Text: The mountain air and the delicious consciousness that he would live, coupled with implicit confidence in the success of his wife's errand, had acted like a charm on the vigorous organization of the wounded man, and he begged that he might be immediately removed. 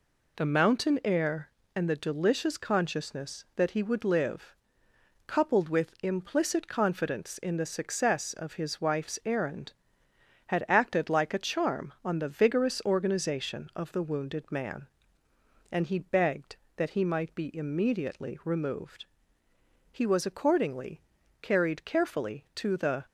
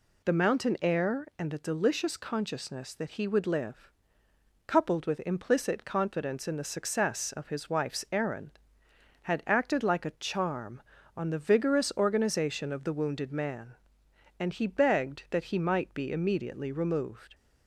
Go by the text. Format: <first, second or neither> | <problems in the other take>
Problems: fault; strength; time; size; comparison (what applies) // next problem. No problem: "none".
second | goes on to say "He was accordingly carried carefully to the"; strong; from 19.9 s on; 3.1 s long